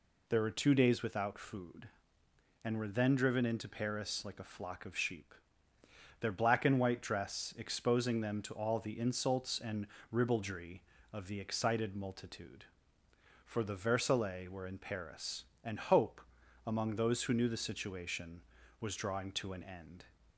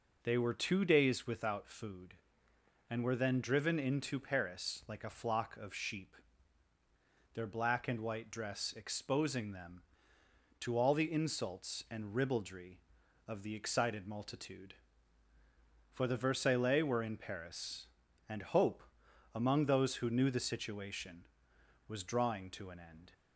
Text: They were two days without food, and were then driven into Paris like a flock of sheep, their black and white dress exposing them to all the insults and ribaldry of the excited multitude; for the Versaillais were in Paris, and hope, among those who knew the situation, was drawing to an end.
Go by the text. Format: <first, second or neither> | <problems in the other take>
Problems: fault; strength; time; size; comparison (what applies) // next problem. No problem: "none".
second | says "There" for "They"; at 0.2 s // pauses between "and" and "ribaldry"; slight; at 9.8 s; 0.24 s long